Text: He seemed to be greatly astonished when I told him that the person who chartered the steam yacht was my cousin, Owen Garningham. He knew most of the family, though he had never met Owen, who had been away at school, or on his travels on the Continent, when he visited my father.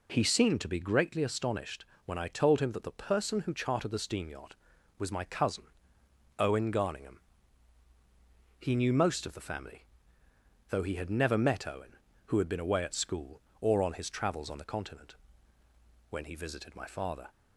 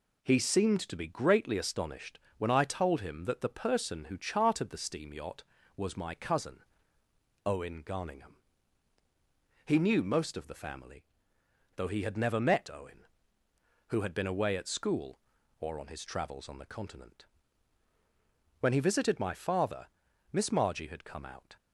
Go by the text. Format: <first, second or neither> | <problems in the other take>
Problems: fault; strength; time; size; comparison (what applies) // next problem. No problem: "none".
first | pauses between "astonished" and "when"; slight; at 2.1 s; 0.20 s long; slight in the first // goes on to say "Miss Margie had come out"; noticeable; from 20.3 s on; 1.2 s long